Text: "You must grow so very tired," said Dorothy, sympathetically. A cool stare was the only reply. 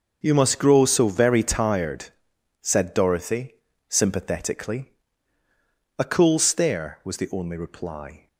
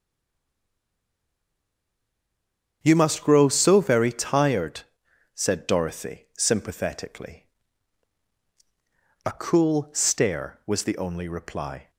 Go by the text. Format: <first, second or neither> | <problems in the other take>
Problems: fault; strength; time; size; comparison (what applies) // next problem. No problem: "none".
first | stays silent before the first word; strong; until 2.8 s; 2.8 s long // starts louder than the rest; strong; until 3.8 s; 8 dB; also in the first